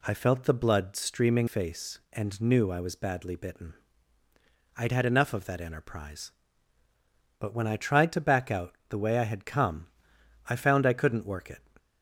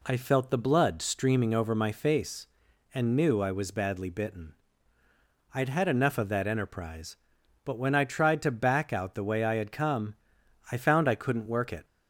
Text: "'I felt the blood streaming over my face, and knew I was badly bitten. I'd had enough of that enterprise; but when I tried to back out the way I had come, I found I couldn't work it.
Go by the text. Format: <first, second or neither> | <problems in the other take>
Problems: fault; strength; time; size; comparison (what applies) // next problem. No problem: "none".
second | skips "over my"; at 1.4 s